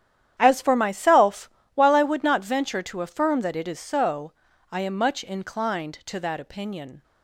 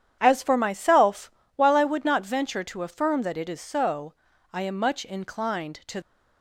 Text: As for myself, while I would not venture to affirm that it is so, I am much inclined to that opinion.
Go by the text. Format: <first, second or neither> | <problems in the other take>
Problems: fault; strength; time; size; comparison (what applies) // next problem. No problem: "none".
first | starts louder than the rest; strong; until 1.2 s; 9.5 dB; strong in the first // stops before "that opinion"; at 6.0 s